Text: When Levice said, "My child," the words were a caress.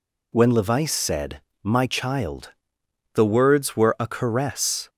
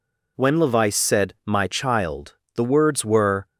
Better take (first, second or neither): first